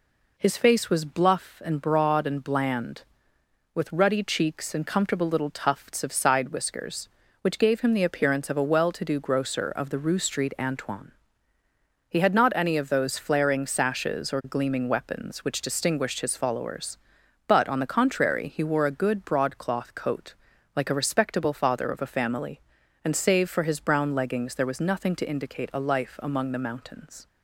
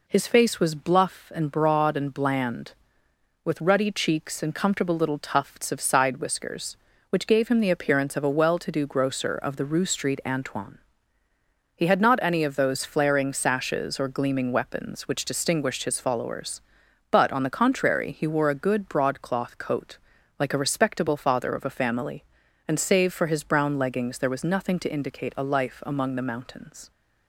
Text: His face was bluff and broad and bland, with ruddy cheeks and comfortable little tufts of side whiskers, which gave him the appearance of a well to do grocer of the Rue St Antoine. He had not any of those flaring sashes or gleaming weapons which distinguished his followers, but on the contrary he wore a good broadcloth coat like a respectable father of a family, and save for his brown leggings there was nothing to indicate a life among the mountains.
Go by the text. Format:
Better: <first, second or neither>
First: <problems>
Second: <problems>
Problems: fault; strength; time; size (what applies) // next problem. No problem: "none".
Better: neither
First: pauses between "coat" and "like"; at 20.3 s; 0.42 s long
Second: pauses between "coat" and "like"; at 19.9 s; 0.42 s long